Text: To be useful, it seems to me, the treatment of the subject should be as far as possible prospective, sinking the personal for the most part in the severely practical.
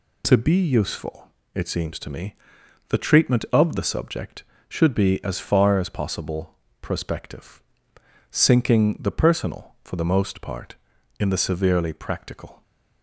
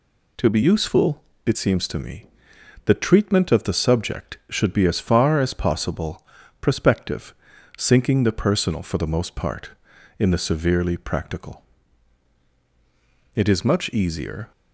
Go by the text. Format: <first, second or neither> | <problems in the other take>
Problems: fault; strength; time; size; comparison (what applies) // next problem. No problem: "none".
first | pauses between "possible" and "prospective"; slight; at 6.2 s; 0.36 s long; slight in the first // goes on to say "It is much easier"; noticeable; from 13.3 s on; 1.1 s long